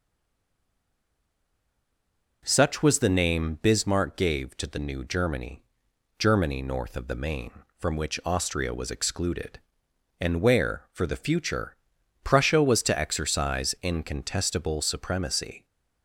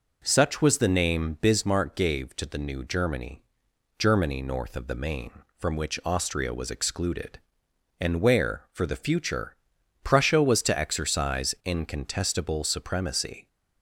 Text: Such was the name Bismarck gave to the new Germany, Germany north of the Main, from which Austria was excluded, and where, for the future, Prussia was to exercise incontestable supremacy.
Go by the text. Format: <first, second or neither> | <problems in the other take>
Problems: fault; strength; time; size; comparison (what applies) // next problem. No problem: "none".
second | stays silent before the first word; until 2.4 s; 2.4 s long